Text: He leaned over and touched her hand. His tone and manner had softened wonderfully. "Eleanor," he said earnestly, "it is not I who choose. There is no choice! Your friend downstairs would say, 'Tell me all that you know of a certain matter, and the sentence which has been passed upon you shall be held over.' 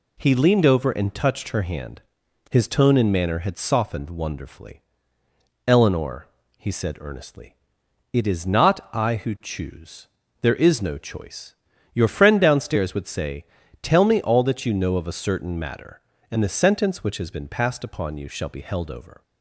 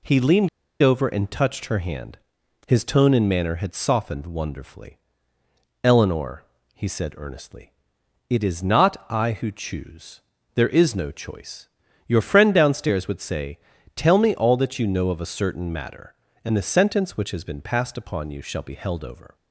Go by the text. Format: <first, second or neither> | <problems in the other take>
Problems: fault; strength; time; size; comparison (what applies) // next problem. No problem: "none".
first | pauses between "leaned" and "over"; slight; at 0.4 s; 0.34 s long